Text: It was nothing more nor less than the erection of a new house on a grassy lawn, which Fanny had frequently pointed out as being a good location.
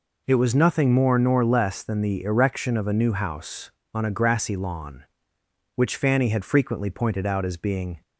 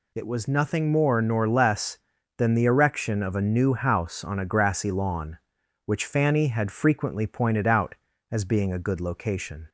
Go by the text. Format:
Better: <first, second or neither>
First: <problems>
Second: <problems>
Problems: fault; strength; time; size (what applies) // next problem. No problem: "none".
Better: second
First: stops before "a good location"; at 8.0 s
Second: none